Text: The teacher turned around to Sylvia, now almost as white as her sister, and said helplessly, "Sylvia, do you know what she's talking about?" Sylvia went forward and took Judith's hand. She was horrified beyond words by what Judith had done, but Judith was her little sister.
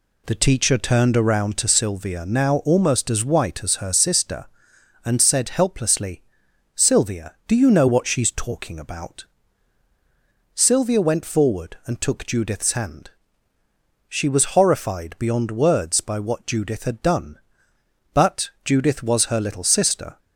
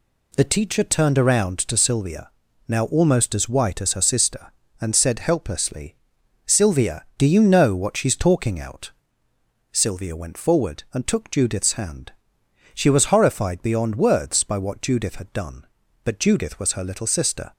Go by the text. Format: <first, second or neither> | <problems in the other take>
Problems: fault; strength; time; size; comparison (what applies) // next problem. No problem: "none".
first | says "out" for "about"; at 8.5 s